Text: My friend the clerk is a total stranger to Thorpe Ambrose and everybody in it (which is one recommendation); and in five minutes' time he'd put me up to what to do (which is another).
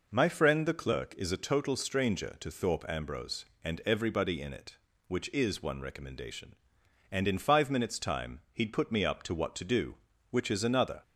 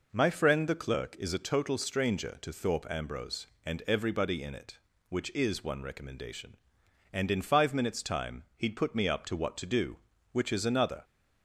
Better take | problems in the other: neither | pauses between "time" and "he'd"; slight; the same in both

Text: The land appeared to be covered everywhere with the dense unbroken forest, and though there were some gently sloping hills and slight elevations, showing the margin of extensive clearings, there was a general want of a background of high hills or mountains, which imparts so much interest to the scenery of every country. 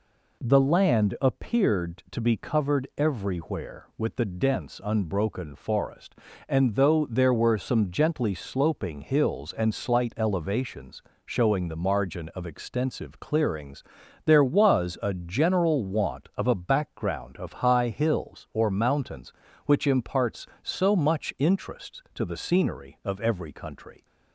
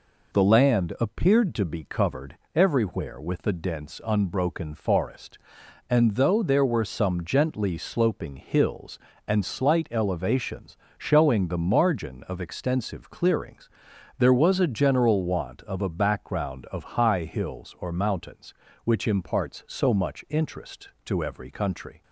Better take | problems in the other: first | pauses between "covered" and "everywhere"; slight; at 2.3 s; 0.18 s long // skips "the scenery of"; at 21.2 s

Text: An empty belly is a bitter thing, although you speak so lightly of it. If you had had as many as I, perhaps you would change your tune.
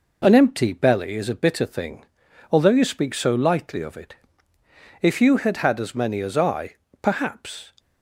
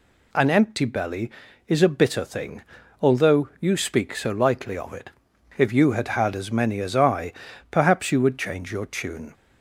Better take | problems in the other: second | stops before "you would change your tune"; at 7.7 s

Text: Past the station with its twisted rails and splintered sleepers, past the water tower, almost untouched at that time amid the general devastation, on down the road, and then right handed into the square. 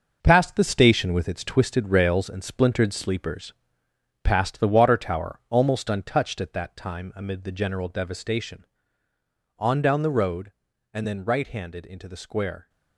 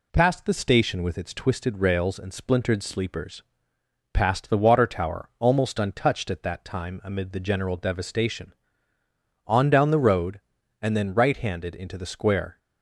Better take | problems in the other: second | gets quieter; strong; throughout; 8.5 dB

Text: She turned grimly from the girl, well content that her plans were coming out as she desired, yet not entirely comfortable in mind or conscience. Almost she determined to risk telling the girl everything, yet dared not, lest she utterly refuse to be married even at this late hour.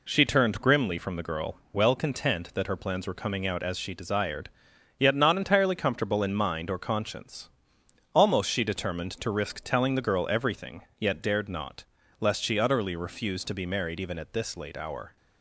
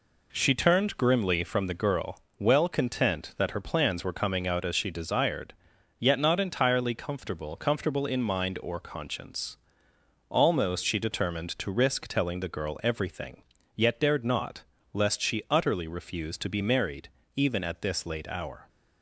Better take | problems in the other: first | says "comfortable" twice; at 7.5 s // pauses between "married" and "even"; slight; at 17.0 s; 0.26 s long

